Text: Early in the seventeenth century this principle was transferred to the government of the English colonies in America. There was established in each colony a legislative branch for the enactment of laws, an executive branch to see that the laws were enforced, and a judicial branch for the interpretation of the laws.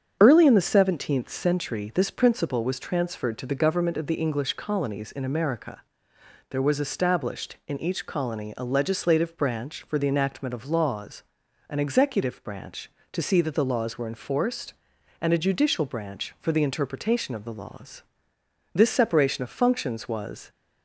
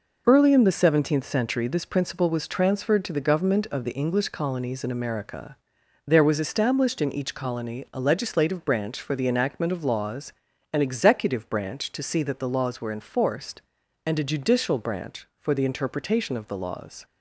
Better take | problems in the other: second | starts louder than the rest; strong; until 1.2 s; 8 dB // goes on to say "This separation of functions was"; strong; from 18.7 s on; 1.7 s long

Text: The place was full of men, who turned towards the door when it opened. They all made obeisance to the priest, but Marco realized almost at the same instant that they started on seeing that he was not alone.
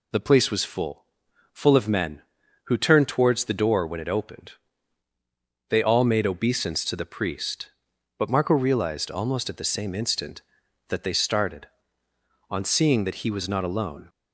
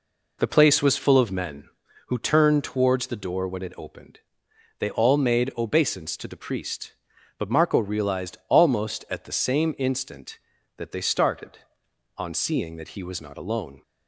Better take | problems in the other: second | says "full" twice; at 1.5 s

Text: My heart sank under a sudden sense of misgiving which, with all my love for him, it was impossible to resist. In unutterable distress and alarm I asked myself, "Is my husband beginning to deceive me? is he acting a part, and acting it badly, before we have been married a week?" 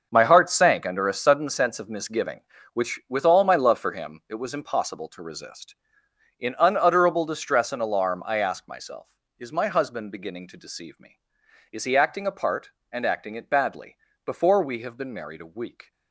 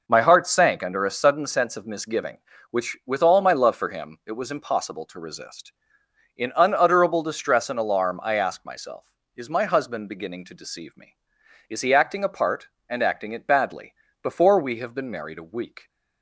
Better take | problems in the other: second | gets quieter; strong; throughout; 12.5 dB

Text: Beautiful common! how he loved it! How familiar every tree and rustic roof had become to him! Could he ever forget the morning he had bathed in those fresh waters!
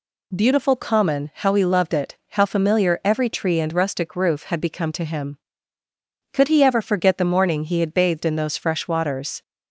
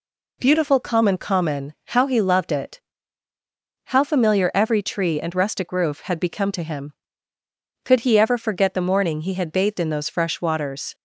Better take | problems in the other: first | says "common" twice; at 1.1 s

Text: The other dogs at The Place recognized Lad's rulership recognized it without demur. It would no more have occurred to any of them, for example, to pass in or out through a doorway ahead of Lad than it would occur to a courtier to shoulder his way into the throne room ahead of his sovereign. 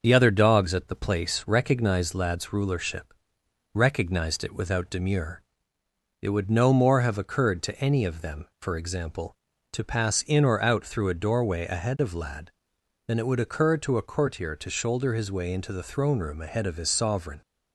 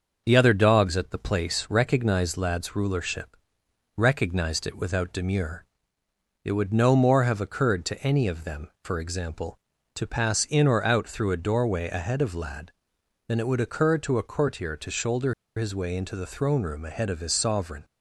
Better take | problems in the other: first | starts louder than the rest; until 1.2 s; 6 dB; also in the first // pauses between "rulership" and "recognized"; noticeable; at 3.3 s; 0.60 s long; noticeable in the first // pauses between "shoulder" and "his"; slight; at 15.3 s; 0.23 s long

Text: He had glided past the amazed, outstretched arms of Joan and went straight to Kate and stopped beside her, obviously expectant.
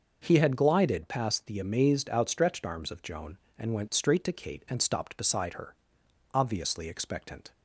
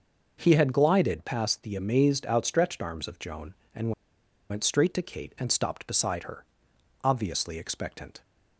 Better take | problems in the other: first | pauses between "and" and "went"; noticeable; at 3.9 s; 0.59 s long

